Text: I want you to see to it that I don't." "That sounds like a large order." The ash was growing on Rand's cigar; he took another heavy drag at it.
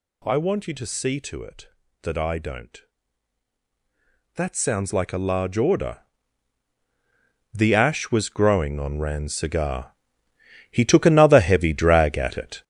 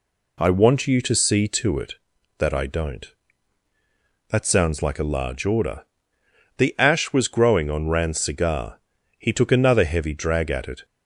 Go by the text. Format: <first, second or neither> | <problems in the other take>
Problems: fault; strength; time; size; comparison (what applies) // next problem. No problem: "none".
second | gets louder; strong; throughout; 7 dB